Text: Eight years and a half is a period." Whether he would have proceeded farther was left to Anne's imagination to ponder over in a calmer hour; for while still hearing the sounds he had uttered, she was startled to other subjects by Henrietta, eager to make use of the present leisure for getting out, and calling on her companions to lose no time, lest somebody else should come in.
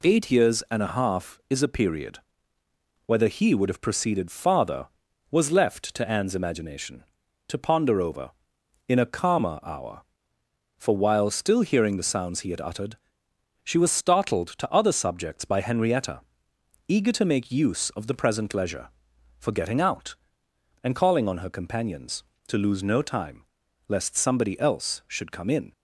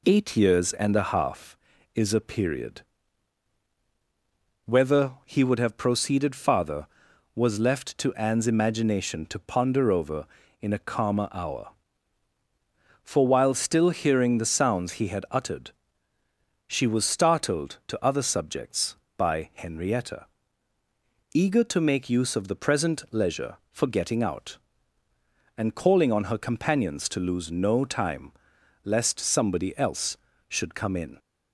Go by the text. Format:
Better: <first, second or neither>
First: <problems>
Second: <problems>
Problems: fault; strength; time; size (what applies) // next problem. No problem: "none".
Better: neither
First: none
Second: none